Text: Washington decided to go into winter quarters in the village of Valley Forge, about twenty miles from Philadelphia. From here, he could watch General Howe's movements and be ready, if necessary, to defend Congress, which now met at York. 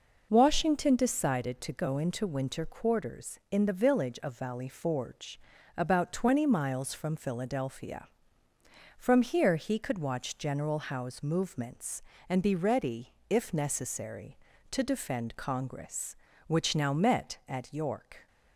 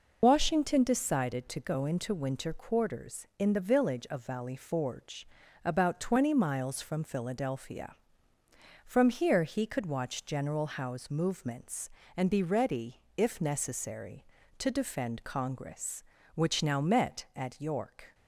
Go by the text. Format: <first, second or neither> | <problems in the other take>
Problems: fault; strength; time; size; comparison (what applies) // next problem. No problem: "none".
first | loses the start of "Washington"; at 0.2 s; 45 ms